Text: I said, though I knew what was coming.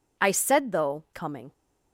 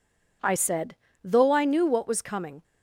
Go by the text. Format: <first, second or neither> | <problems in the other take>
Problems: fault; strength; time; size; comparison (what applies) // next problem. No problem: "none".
second | skips "I knew what was"; at 1.0 s